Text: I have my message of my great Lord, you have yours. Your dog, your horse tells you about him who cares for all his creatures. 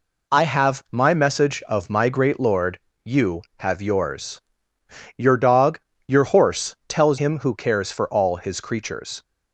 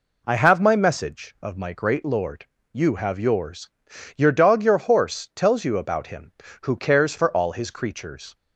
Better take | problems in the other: second | skips "you about"; at 7.1 s

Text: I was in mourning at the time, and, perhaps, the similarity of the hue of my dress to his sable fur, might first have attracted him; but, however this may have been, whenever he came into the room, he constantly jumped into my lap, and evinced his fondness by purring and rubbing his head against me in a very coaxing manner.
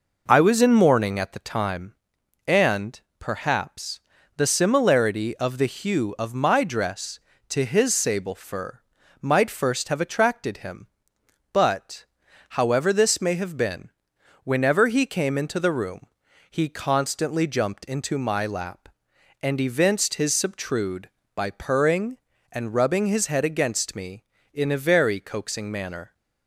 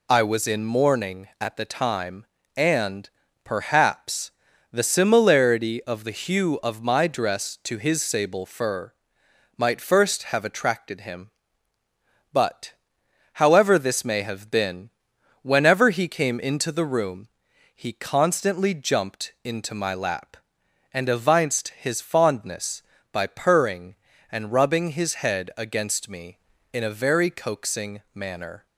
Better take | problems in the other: second | says "subtrude" for "fondness"; at 20.3 s

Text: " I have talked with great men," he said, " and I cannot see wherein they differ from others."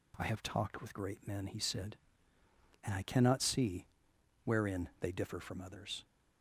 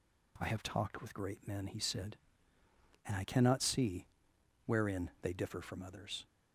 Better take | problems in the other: neither | pauses between "see" and "wherein"; noticeable; the same in both

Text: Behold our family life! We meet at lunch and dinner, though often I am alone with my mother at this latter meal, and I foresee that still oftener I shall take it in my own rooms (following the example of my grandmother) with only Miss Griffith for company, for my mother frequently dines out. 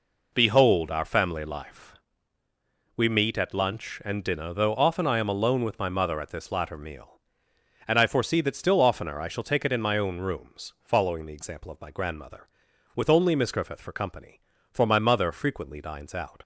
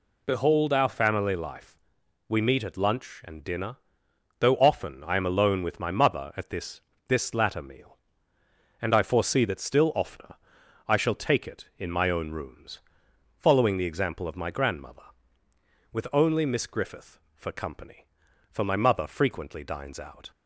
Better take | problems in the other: first | says "this" twice; at 7.0 s // pauses between "oftener" and "I"; noticeable; at 10.3 s; 0.52 s long

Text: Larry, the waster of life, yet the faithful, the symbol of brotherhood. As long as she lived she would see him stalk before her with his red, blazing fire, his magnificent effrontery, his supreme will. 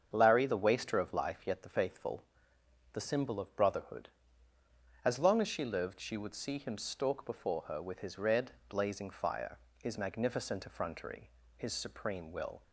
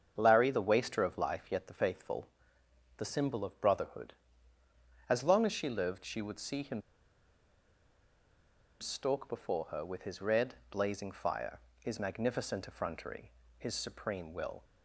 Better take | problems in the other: first | starts louder than the rest; strong; until 1.1 s; 7.5 dB; strong in the first // pauses between "him" and "stalk"; strong; at 6.8 s; 1.9 s long

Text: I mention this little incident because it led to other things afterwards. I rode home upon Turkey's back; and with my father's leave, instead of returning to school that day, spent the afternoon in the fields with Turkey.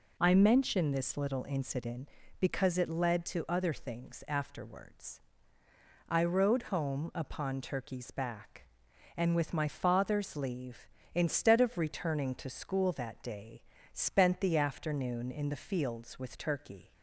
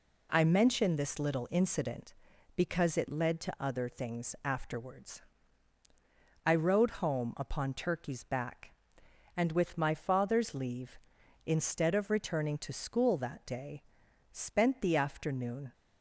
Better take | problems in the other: first | stops before "in the fields with Turkey"; at 15.7 s

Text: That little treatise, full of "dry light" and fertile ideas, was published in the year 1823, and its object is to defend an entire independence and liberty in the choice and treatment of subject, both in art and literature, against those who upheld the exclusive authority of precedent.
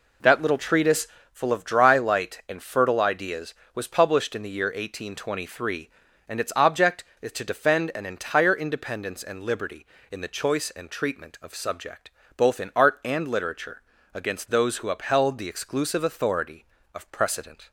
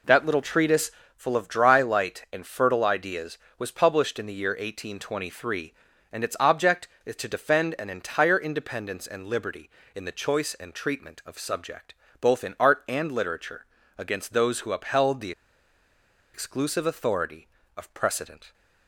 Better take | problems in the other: first | pauses between "the" and "exclusive"; at 15.3 s; 1.0 s long

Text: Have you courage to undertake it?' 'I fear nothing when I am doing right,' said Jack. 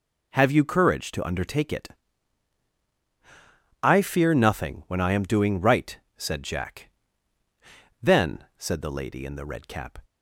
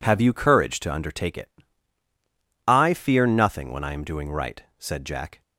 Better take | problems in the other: second | goes on to say "Then said the lady in the red cap"; strong; from 8.0 s on; 1.9 s long

